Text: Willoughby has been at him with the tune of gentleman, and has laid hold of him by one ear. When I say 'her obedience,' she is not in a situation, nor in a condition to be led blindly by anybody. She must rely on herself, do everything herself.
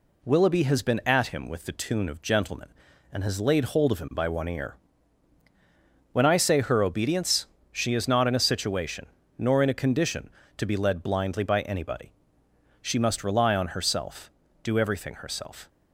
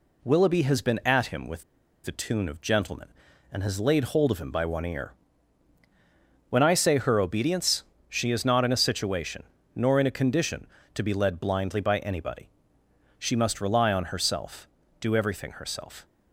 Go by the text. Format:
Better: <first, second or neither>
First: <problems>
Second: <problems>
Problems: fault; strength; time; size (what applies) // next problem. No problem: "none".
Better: first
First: none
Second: pauses between "with" and "the"; at 1.6 s; 0.41 s long